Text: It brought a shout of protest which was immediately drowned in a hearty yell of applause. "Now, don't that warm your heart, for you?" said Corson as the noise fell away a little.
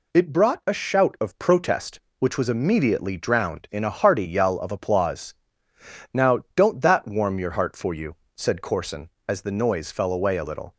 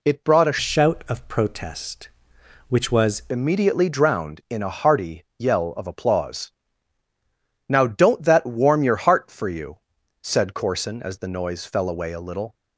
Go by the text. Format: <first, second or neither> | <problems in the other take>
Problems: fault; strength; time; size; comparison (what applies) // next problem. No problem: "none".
first | changes voice from "shout" to "was"; from 0.5 to 3.2 s; 2.7 s long // pauses between "hearty" and "yell"; slight; at 5.2 s; 0.16 s long